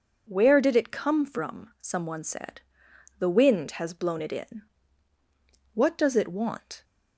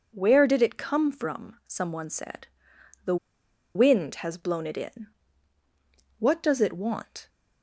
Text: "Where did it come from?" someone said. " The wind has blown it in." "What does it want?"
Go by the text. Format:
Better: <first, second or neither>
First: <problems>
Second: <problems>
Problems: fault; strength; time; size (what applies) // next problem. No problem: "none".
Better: first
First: none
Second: pauses between "The" and "wind"; noticeable; at 3.1 s; 0.59 s long